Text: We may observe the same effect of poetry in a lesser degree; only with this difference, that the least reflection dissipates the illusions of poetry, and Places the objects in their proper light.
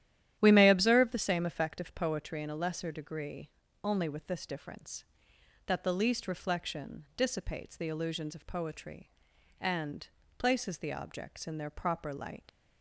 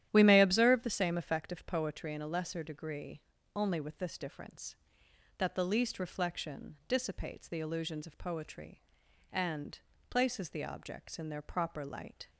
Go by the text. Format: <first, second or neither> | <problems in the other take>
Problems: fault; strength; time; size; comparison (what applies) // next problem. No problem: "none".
second | starts louder than the rest; strong; until 1.4 s; 11.5 dB; strong in the second // pauses between "and" and "Places"; slight; at 10.0 s; 0.28 s long; slight in the second // leaves "light" unfinished; at 12.4 s; 85 ms